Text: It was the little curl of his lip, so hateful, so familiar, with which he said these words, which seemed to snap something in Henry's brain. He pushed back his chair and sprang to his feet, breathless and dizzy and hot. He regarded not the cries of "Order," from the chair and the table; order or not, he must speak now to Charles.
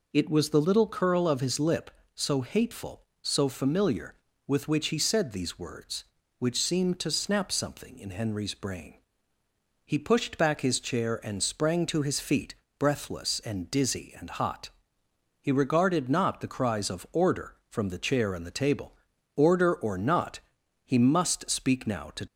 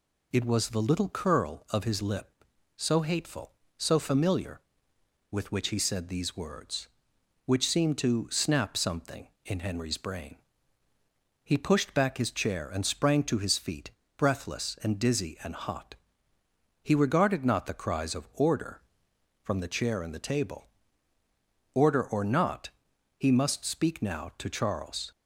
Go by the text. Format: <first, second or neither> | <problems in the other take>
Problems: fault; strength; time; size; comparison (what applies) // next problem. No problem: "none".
second | stops before "Charles"; at 22.2 s